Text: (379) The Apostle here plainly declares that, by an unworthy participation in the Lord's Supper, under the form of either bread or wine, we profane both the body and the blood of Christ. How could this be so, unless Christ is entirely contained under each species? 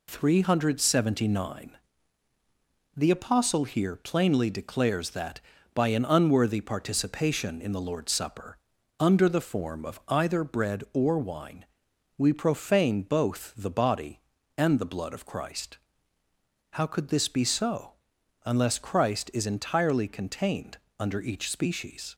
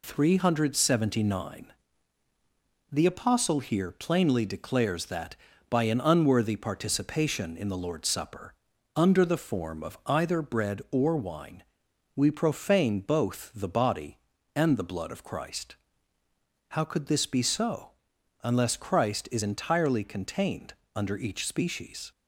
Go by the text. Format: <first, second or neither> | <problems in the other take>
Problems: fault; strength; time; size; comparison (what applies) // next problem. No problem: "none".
neither | pauses between "contained" and "under"; slight; the same in both